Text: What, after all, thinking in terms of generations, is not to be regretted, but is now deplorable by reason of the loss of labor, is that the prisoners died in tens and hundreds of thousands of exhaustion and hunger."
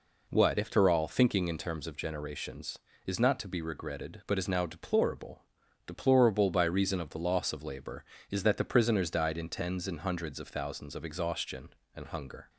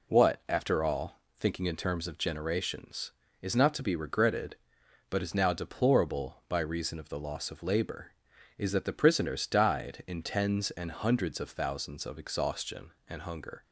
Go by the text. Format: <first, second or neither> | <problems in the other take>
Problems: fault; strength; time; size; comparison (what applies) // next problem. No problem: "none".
second | says "deplorable" twice; at 5.8 s